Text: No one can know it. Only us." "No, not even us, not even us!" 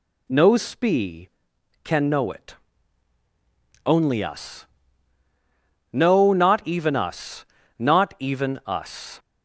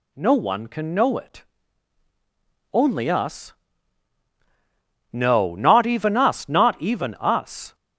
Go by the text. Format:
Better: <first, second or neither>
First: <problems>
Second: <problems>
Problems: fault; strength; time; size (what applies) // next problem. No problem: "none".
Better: second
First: says "spee" for "one"; at 0.5 s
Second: none